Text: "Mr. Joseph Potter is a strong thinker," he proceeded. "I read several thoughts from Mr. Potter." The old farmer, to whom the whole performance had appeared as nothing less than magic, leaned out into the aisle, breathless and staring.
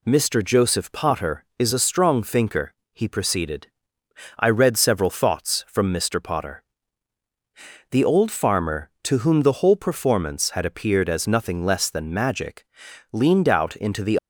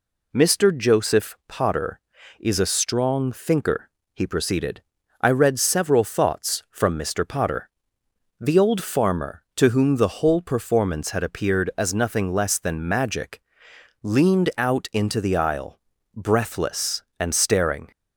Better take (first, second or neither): second